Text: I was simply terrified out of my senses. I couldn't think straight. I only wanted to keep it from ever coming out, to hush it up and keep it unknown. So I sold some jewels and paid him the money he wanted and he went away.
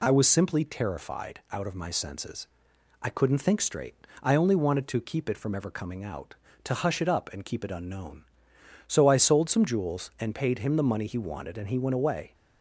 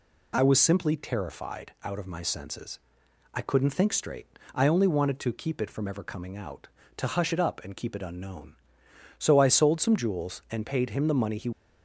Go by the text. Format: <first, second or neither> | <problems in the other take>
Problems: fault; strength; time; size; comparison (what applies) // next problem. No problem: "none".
first | stops before "wanted and he went away"; at 11.5 s